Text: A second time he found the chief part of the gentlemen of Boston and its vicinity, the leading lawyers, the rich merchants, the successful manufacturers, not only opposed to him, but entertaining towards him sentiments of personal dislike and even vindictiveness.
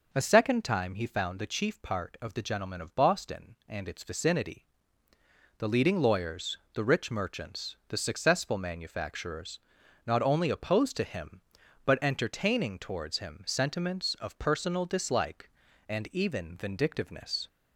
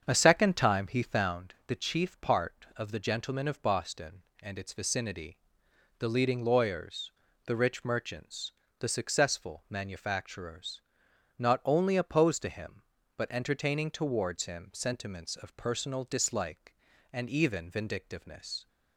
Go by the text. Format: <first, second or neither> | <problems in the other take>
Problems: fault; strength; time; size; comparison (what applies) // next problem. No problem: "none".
first | starts louder than the rest; strong; until 1.5 s; 7.5 dB